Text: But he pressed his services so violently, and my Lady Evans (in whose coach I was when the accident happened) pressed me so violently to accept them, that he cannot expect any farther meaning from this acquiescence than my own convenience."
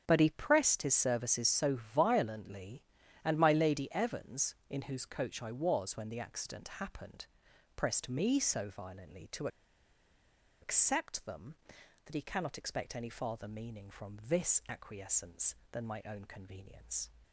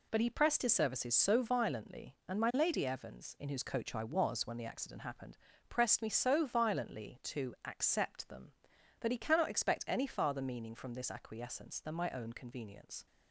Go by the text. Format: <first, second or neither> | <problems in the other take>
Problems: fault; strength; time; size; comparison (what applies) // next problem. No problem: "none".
second | starts louder than the rest; strong; until 1.0 s; 7.5 dB // pauses between "to" and "accept"; at 9.4 s; 1.1 s long